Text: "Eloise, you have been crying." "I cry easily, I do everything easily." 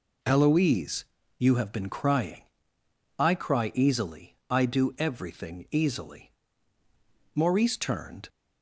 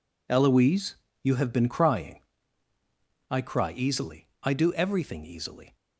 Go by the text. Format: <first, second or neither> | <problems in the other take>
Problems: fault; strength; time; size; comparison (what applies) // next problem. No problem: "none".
second | goes on to say "Maurice turned"; noticeable; from 7.3 s on; 0.94 s long